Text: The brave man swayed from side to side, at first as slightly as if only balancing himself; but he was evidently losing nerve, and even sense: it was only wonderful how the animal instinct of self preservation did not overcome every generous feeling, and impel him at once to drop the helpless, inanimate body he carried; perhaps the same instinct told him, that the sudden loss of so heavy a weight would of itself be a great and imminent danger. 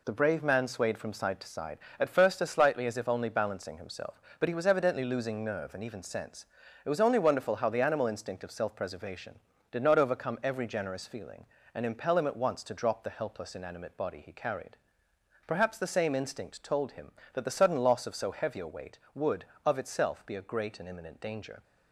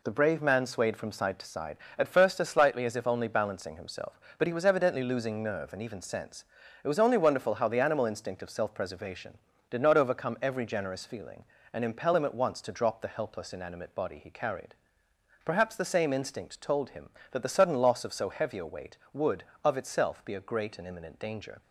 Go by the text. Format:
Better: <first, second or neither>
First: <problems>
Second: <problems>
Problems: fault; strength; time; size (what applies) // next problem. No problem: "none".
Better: neither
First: none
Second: none